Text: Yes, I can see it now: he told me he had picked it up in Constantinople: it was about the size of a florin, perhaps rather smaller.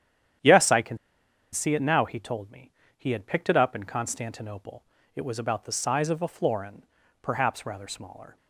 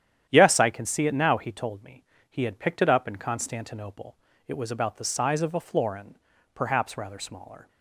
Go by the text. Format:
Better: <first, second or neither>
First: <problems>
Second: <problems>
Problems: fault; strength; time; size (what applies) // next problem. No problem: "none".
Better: second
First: starts louder than the rest; strong; until 1.9 s; 10 dB // pauses between "can" and "see"; noticeable; at 0.9 s; 0.55 s long // pauses between "me" and "he"; slight; at 2.7 s; 0.26 s long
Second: starts louder than the rest; strong; until 1.3 s; 10 dB // pauses between "me" and "he"; slight; at 2.0 s; 0.26 s long